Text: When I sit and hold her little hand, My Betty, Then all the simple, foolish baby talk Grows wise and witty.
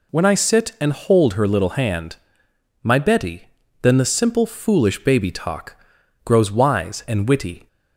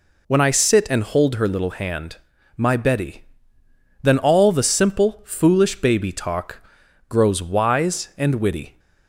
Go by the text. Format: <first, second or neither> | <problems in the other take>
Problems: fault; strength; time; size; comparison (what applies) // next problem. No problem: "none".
second | skips "all"; at 3.9 s // pauses between "talk" and "Grows"; noticeable; at 5.7 s; 0.48 s long; noticeable in the second